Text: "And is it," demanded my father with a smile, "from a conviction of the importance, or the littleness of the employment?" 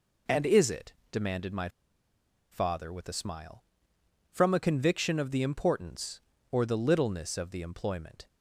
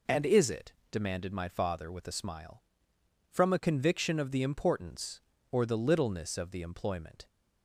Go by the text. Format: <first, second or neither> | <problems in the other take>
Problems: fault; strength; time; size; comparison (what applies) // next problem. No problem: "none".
second | pauses between "my" and "father"; noticeable; at 1.6 s; 0.83 s long